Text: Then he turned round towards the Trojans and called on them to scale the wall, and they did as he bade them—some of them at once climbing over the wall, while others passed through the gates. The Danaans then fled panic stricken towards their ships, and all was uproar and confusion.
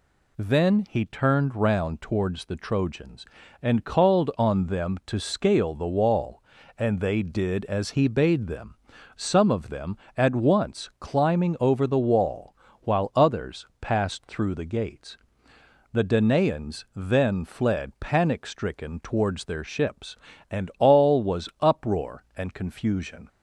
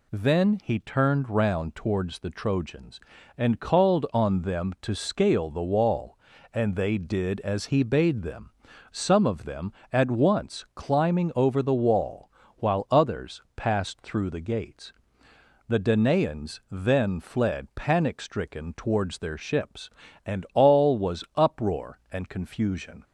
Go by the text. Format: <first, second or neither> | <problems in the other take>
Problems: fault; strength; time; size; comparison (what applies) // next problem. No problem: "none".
neither | none